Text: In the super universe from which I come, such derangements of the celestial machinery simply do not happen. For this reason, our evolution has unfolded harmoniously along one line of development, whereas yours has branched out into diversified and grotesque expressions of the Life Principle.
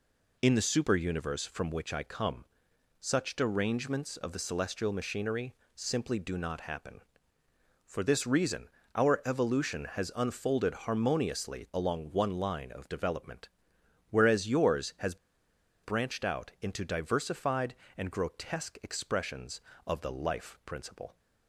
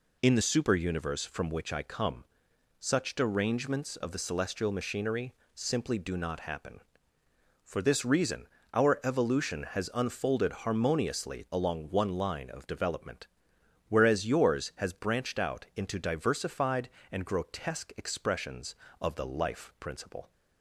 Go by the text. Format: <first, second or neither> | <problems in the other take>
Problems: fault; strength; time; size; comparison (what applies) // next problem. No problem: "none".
second | pauses between "machinery" and "simply"; slight; at 5.5 s; 0.22 s long; slight in the second // pauses between "has" and "branched"; noticeable; at 15.1 s; 0.66 s long